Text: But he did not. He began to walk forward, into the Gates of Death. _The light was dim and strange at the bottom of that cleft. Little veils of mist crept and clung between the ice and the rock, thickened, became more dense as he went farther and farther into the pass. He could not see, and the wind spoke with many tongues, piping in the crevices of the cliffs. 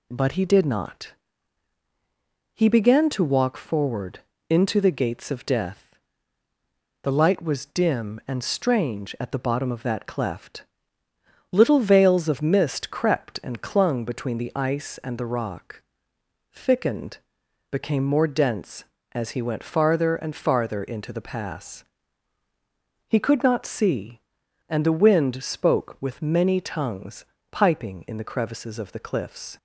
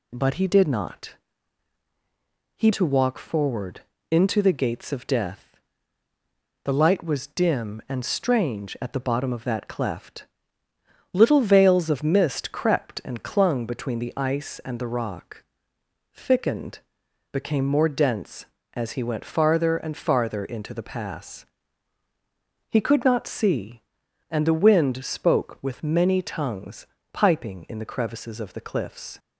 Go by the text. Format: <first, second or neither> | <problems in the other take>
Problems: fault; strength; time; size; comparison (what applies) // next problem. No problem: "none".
first | skips "began"; at 2.7 s